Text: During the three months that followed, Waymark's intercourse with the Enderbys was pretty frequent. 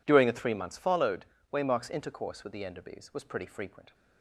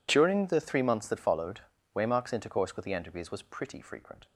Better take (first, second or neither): second